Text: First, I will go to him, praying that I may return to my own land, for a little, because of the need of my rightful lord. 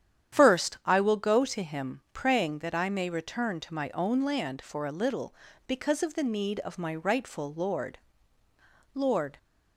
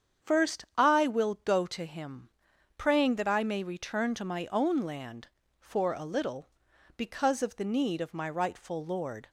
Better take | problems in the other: second | starts louder than the rest; strong; until 1.4 s; 9.5 dB; strong in the second // says "lord" twice; at 8.9 s

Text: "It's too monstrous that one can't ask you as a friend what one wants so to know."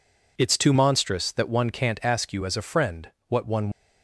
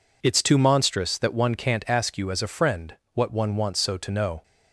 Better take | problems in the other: second | pauses between "friend" and "what"; slight; at 3.1 s; 0.16 s long; slight in the second // stops before "wants so to know"; at 3.7 s

